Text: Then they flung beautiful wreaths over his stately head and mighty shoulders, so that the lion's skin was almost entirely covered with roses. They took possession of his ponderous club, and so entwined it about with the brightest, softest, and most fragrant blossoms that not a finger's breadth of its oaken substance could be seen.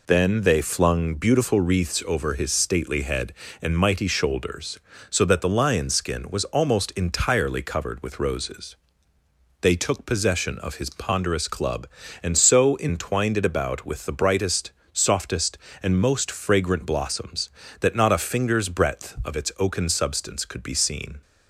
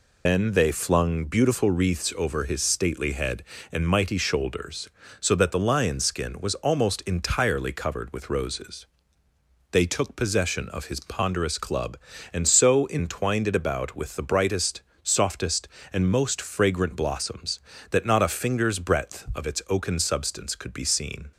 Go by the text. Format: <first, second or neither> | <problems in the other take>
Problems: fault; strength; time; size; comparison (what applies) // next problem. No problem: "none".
first | loses the start of "Then"; at 0.2 s; 80 ms